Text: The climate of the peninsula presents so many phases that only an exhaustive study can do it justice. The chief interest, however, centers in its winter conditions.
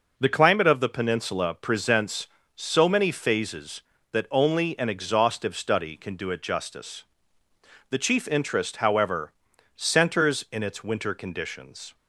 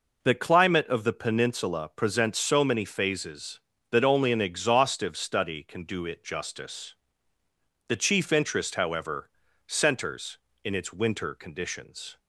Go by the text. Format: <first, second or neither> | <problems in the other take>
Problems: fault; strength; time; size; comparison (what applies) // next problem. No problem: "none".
neither | none